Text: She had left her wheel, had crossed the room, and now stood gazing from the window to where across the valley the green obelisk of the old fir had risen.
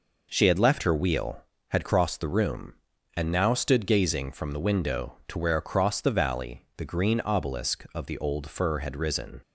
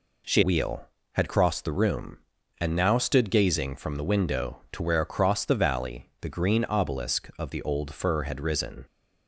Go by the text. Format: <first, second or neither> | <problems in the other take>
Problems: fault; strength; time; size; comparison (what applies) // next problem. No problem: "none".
first | skips "had left her"; at 0.4 s